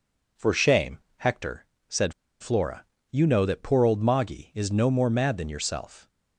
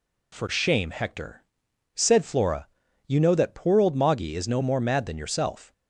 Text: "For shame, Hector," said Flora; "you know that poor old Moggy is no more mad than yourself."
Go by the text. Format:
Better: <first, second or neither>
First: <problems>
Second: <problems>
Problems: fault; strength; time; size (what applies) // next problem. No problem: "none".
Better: second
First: pauses between "said" and "Flora"; slight; at 2.1 s; 0.28 s long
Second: none